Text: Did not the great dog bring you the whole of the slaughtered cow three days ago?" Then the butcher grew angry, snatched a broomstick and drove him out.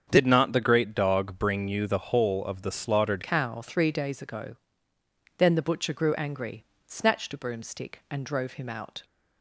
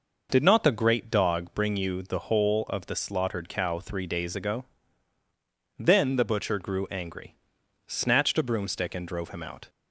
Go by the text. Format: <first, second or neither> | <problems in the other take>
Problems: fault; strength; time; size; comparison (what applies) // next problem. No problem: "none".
second | starts louder than the rest; strong; until 1.1 s; 7.5 dB // changes voice at "cow"; from 3.2 s on; 5.8 s long